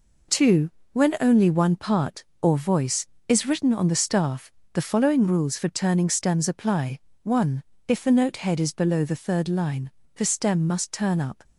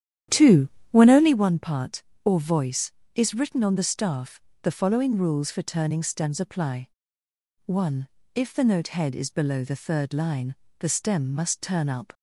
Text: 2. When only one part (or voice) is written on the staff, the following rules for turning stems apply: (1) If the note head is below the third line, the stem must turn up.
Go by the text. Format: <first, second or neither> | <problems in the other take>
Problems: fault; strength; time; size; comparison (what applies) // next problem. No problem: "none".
first | starts louder than the rest; strong; until 1.4 s; 10.5 dB